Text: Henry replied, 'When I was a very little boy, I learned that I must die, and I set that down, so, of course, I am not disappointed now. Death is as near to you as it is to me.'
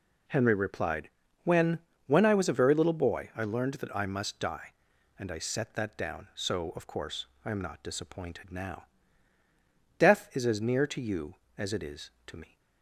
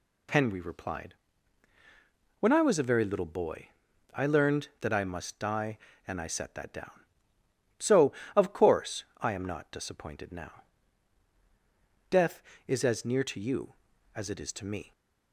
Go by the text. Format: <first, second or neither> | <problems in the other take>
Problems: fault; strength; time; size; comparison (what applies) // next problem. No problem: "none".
second | says "When" twice; at 2.0 s